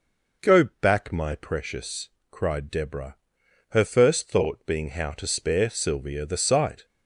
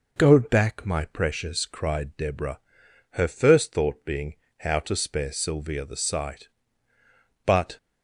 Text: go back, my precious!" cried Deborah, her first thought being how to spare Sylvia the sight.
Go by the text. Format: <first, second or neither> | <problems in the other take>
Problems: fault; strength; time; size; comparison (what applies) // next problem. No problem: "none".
first | pauses between "being" and "how"; slight; at 4.3 s; 0.24 s long // goes on to say "But"; slight; from 7.4 s on; 0.32 s long